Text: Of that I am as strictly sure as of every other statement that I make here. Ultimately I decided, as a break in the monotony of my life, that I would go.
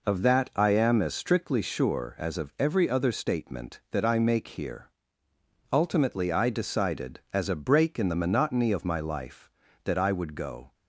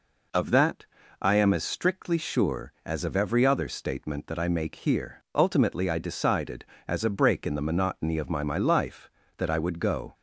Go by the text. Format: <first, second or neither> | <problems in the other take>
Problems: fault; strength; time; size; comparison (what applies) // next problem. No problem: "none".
first | pauses between "that" and "I"; slight; at 0.8 s; 0.34 s long // says "my" twice; at 8.4 s